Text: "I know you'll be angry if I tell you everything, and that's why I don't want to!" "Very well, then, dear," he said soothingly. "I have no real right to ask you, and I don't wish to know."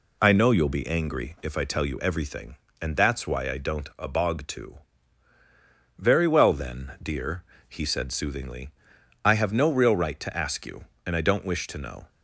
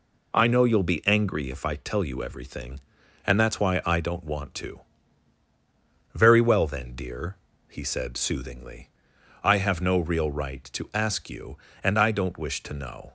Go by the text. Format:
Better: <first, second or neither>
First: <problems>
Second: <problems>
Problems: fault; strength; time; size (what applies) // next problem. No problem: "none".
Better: second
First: says "abog" for "want"; at 3.9 s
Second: none